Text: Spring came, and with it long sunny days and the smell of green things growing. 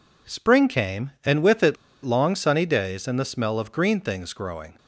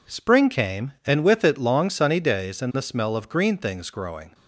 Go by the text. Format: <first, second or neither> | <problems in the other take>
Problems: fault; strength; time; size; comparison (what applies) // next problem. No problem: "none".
second | pauses between "it" and "long"; slight; at 1.7 s; 0.27 s long